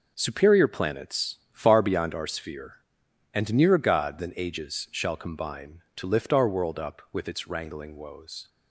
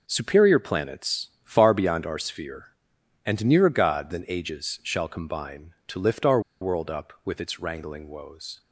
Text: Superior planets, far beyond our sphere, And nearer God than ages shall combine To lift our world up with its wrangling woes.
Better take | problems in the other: first | pauses between "our" and "world"; slight; at 6.3 s; 0.21 s long

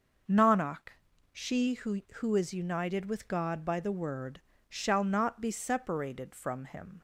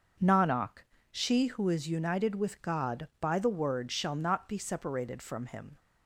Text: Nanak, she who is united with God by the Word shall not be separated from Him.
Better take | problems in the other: second | starts louder than the rest; until 1.6 s; 6 dB; also in the second // says "who" twice; at 2.1 s // pauses between "Word" and "shall"; slight; at 4.4 s; 0.28 s long

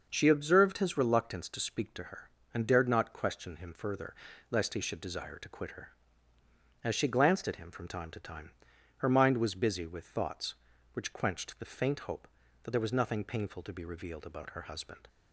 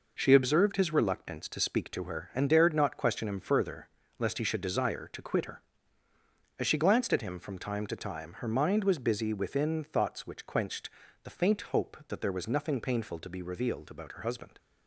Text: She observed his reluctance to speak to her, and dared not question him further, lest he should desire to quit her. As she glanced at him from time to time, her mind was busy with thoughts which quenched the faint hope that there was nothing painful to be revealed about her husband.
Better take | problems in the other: first | says "within" for "with"; at 9.3 s // pauses between "quenched" and "the"; slight; at 10.8 s; 0.32 s long

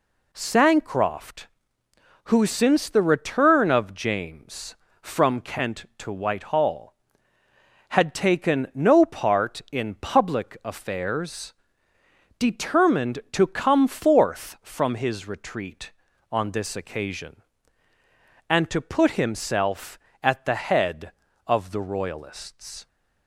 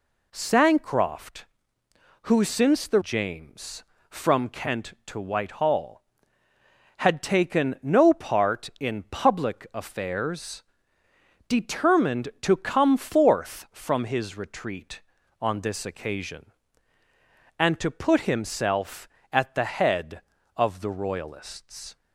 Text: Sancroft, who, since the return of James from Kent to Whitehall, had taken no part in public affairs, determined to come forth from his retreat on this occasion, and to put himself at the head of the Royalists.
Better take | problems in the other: first | skips "return of"; at 3.0 s

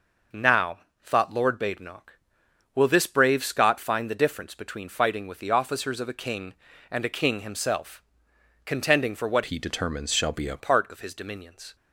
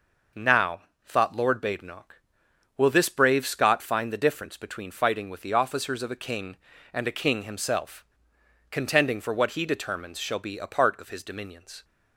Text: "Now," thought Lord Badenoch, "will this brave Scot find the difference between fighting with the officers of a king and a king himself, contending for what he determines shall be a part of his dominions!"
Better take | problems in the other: second | changes voice from "he" to "a"; from 9.4 to 10.5 s; 1.1 s long

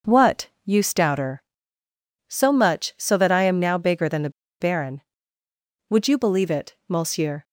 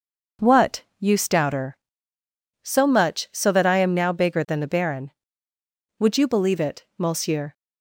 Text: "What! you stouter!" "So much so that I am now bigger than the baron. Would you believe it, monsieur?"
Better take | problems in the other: second | pauses between "the" and "baron"; slight; at 4.2 s; 0.30 s long

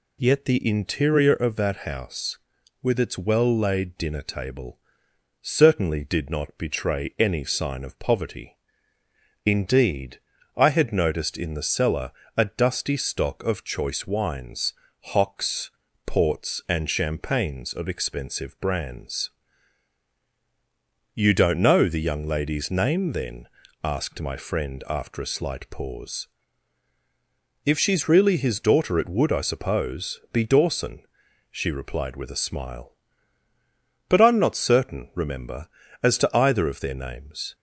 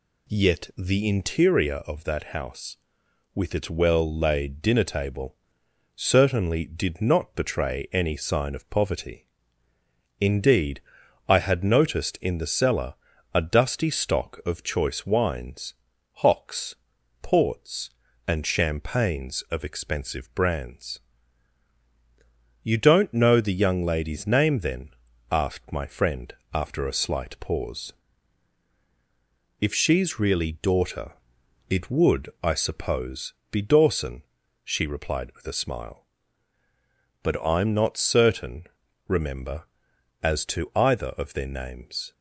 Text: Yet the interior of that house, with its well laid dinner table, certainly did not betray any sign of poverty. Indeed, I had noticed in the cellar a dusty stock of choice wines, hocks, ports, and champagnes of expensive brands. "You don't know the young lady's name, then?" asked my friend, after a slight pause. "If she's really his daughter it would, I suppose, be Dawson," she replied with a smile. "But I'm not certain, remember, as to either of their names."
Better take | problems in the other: first | pauses between "cellar" and "a"; at 12.9 s; 0.40 s long; slight in the first // skips "his"; at 30.5 s // pauses between "daughter" and "it"; noticeable; at 31.1 s; 0.56 s long

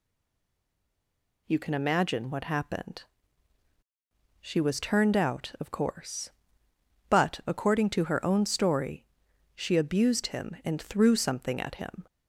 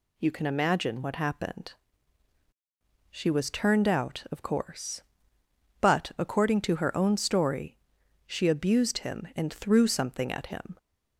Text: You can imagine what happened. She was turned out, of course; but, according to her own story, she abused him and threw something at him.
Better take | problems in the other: second | stays silent before the first word; noticeable; until 1.4 s; 1.4 s long

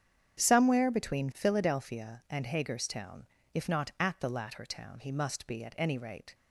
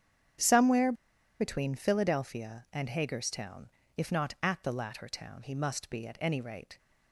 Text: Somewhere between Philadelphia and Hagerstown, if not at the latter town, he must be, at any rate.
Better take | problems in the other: first | starts louder than the rest; strong; until 1.8 s; 9 dB; strong in the first // pauses between "Somewhere" and "between"; noticeable; at 0.9 s; 0.46 s long

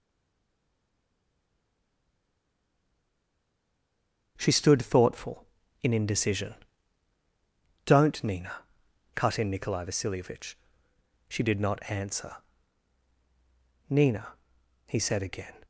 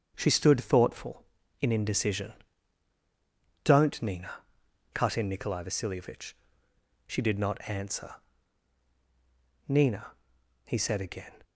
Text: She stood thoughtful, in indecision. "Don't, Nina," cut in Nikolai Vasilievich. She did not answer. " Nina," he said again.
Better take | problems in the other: second | stays silent before the first word; strong; until 4.3 s; 4.3 s long // starts louder than the rest; strong; until 5.3 s; 8.5 dB; strong in the second

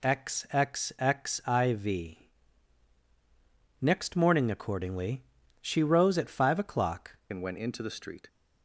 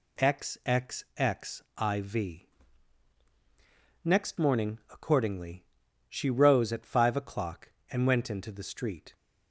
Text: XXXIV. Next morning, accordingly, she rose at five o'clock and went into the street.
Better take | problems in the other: second | changes voice at "and"; from 7.3 s on; 0.9 s long

